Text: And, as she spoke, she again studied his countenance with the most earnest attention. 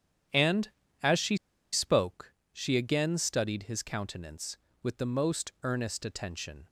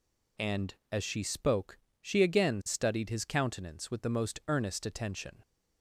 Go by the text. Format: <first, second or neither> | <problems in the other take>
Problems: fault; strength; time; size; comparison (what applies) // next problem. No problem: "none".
second | starts louder than the rest; strong; until 2.0 s; 10 dB // pauses between "she" and "spoke"; at 1.3 s; 0.36 s long